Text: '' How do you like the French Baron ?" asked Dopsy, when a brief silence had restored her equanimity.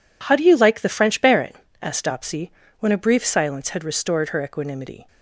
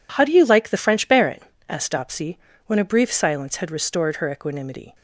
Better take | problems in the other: neither | none

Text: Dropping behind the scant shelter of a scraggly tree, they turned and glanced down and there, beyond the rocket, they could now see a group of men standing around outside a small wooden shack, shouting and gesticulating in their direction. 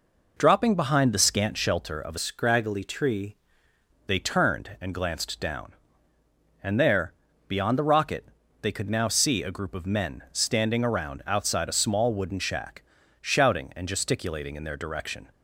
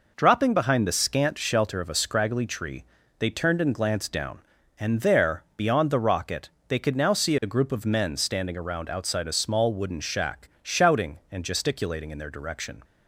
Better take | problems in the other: second | changes voice from "scraggly" to "tree"; from 2.1 to 3.3 s; 1.2 s long

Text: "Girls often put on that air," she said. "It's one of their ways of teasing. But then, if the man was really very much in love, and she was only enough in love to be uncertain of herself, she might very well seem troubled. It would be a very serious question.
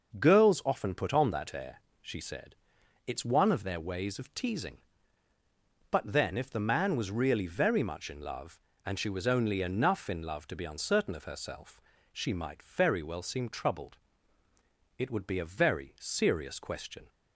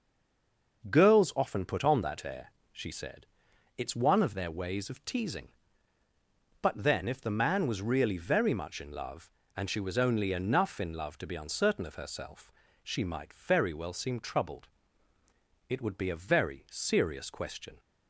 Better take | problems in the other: first | stays silent before the first word; slight; until 0.8 s; 0.8 s long // starts louder than the rest; until 1.9 s; 6.5 dB; also in the first

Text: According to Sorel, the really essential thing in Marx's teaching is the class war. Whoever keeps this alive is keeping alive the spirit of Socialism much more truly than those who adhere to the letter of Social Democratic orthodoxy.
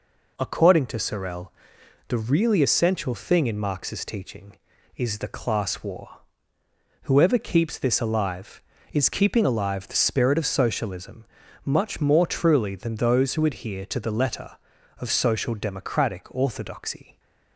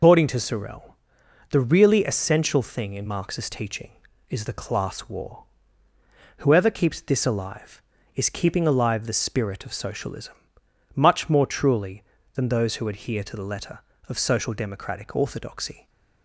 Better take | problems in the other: first | loses the start of "According"; at 0.0 s; 160 ms // pauses between "Socialism" and "much"; noticeable; at 10.3 s; 0.60 s long; also in the first

